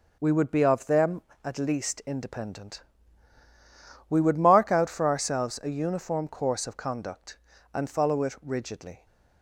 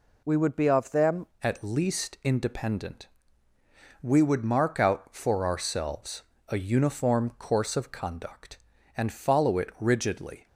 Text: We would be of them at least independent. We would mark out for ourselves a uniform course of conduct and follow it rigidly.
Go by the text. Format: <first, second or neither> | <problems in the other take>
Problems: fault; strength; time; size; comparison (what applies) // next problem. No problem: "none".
first | changes voice at "at"; from 1.4 s on; 9.0 s long // pauses between "ourselves" and "a"; slight; at 6.2 s; 0.26 s long